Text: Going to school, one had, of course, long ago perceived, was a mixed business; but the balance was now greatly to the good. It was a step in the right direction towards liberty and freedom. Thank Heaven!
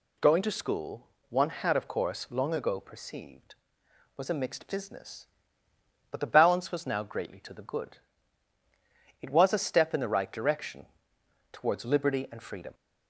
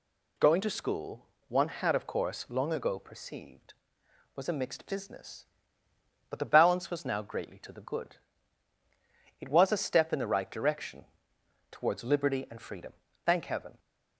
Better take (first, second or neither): second